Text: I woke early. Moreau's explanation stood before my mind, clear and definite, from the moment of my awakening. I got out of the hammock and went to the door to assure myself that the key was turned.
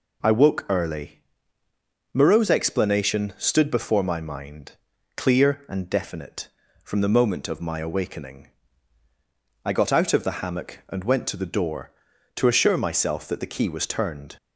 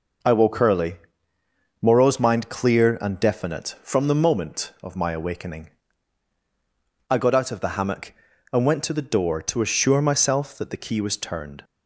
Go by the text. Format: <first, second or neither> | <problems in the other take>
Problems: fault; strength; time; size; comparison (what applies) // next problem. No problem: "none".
first | skips "explanation stood before my"; at 2.1 s